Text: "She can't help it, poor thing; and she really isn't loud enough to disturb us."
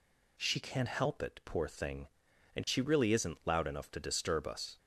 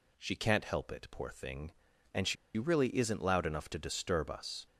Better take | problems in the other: first | pauses between "she" and "really"; slight; at 2.3 s; 0.22 s long

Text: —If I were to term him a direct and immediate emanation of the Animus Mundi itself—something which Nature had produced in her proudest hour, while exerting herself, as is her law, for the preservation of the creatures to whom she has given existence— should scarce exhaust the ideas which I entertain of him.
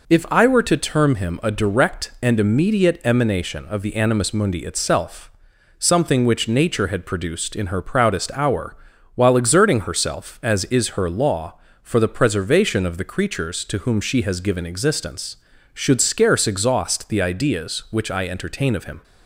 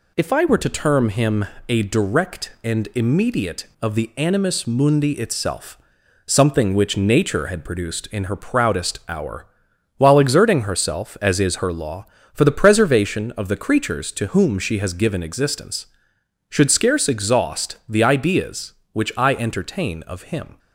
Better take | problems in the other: first | pauses between "him" and "a"; slight; at 1.4 s; 0.24 s long // skips "emanation"; at 3.7 s

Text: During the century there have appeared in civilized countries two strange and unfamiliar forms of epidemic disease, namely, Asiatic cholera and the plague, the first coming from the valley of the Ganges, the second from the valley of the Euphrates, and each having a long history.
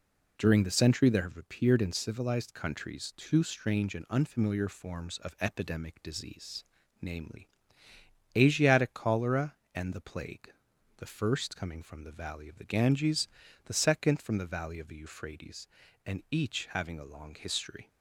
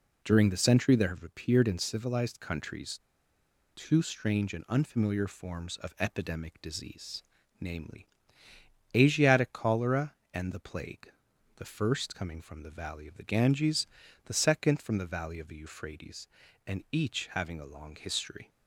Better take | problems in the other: first | pauses between "countries" and "two"; noticeable; at 2.9 s; 0.76 s long

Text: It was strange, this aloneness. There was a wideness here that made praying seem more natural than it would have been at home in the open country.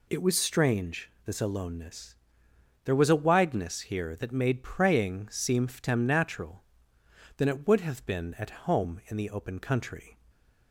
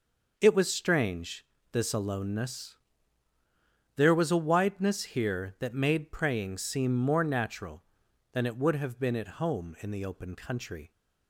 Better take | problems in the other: second | says "ftem" for "more"; at 5.6 s // stays silent after the last word; slight; from 10.1 s on; 0.6 s long

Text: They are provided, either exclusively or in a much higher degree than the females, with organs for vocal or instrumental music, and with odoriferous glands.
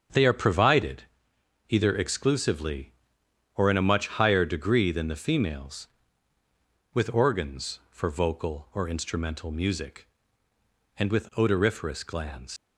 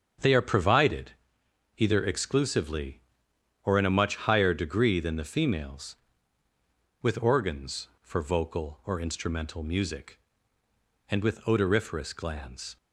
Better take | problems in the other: second | starts louder than the rest; strong; until 1.7 s; 7 dB; strong in the second // leaves "glands" unfinished; at 12.5 s; 105 ms

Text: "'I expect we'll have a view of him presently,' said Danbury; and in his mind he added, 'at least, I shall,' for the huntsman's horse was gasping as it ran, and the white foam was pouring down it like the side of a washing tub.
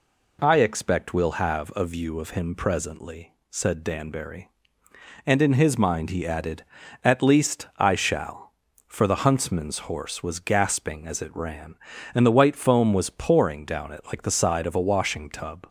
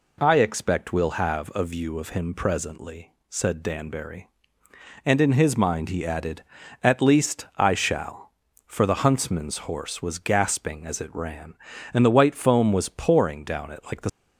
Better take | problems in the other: first | stops before "side of a washing tub"; at 14.0 s

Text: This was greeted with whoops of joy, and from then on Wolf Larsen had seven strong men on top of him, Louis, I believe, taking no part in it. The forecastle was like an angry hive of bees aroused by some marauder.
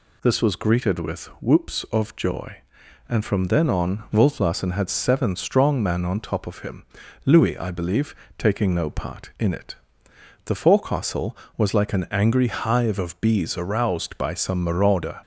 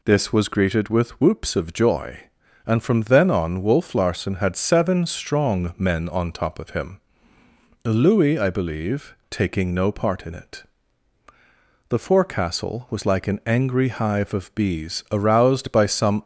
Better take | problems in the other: first | stops before "marauder"; at 16.2 s

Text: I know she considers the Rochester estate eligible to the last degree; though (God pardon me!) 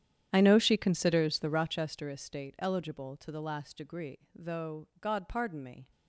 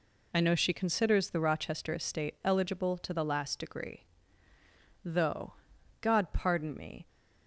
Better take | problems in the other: second | starts louder than the rest; strong; until 1.9 s; 10 dB

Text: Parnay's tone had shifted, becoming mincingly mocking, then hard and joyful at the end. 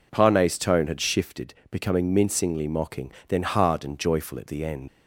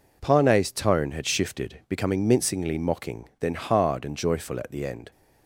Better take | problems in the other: second | leaves "end" unfinished; at 4.8 s; 80 ms

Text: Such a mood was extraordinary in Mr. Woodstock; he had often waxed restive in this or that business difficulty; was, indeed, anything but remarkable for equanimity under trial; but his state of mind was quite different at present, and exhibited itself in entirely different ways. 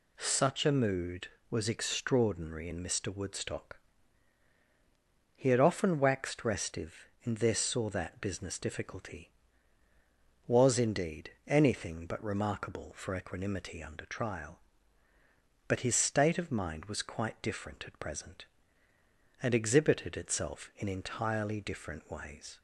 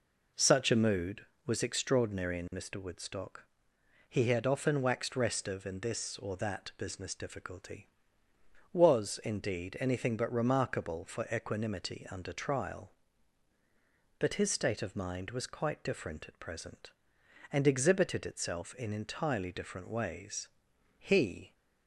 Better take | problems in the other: first | goes on to say "He"; from 20.9 s on; 0.54 s long

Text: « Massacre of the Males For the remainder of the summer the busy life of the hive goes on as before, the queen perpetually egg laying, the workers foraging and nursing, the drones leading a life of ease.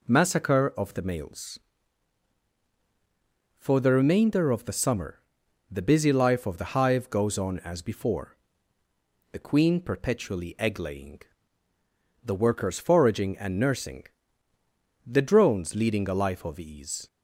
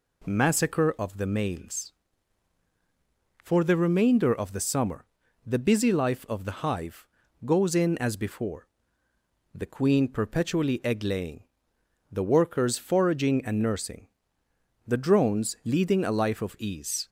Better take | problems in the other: first | pauses between "summer" and "the"; at 5.0 s; 0.40 s long; noticeable in the first // pauses between "hive" and "goes"; slight; at 7.0 s; 0.36 s long // says "in" for "on"; at 7.7 s

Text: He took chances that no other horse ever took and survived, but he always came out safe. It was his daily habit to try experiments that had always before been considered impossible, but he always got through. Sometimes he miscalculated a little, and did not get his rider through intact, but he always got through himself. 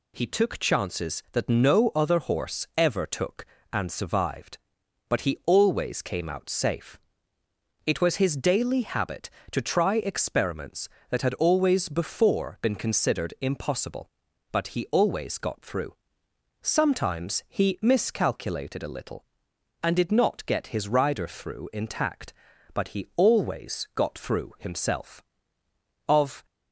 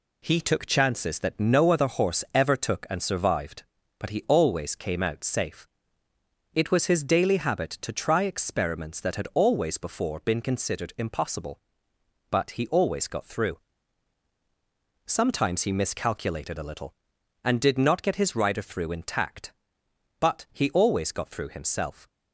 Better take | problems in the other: second | goes on to say "Of"; slight; from 26.0 s on; 0.38 s long

